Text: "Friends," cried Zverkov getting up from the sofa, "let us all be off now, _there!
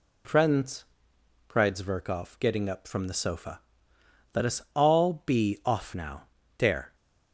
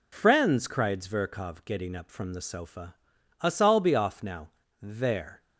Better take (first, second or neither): first